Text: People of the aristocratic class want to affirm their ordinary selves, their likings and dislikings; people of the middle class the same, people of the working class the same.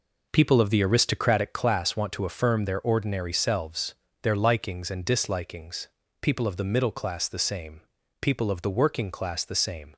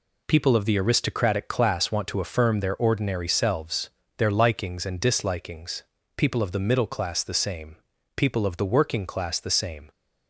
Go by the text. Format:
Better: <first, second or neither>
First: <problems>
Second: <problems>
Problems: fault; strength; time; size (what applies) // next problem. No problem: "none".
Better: second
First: starts louder than the rest; noticeable; until 1.6 s; 5 dB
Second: none